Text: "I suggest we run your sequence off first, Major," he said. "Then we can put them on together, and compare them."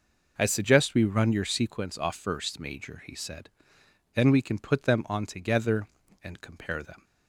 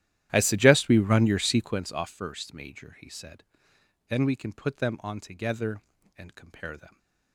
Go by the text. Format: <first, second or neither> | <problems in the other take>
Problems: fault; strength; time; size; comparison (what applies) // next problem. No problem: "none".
first | starts louder than the rest; strong; until 2.1 s; 12.5 dB